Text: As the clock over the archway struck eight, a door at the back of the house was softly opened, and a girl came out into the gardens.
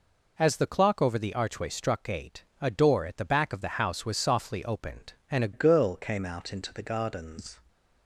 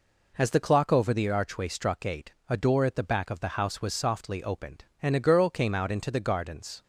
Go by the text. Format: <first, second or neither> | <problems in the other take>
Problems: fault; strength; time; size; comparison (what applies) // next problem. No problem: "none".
second | changes voice at "girl"; from 5.5 s on; 2.0 s long